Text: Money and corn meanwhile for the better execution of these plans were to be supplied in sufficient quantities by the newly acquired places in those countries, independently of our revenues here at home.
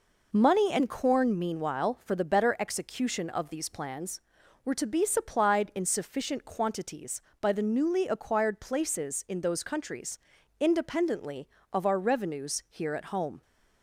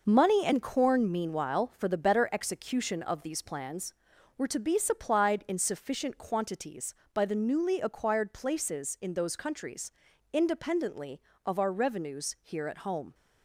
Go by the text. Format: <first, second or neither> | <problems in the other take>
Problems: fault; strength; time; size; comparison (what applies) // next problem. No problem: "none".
first | gets quieter; strong; throughout; 8 dB